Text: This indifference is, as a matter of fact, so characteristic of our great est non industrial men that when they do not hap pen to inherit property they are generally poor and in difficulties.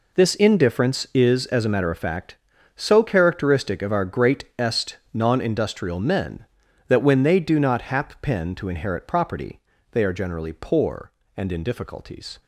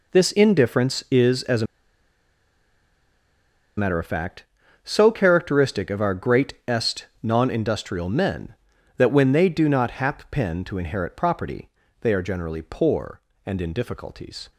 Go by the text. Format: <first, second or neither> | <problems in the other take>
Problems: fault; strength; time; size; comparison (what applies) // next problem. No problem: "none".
first | pauses between "a" and "matter"; strong; at 1.6 s; 2.1 s long // pauses between "est" and "non"; slight; at 7.0 s; 0.16 s long; slight in the first // pauses between "property" and "they"; slight; at 11.6 s; 0.32 s long; slight in the first